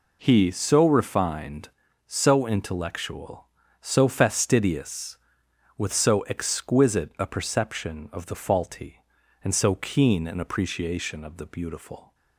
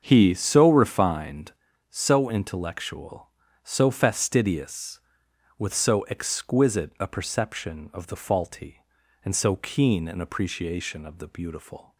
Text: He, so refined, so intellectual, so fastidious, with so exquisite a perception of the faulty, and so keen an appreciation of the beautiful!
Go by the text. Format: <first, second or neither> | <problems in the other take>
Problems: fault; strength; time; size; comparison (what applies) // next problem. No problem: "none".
first | starts louder than the rest; until 1.4 s; 7 dB